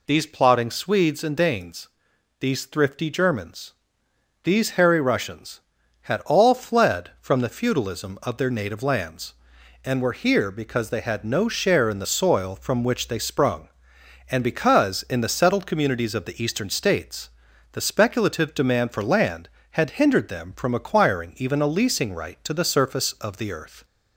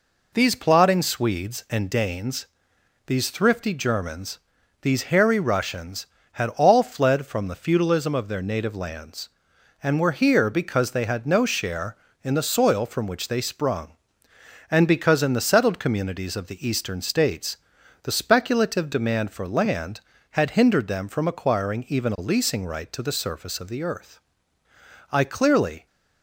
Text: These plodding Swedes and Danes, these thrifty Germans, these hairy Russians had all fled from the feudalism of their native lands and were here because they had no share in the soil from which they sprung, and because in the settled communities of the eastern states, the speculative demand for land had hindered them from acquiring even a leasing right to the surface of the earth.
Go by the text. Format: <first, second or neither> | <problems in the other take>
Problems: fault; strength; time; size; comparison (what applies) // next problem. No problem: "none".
first | goes on to say "I clearly"; noticeable; from 25.0 s on; 0.76 s long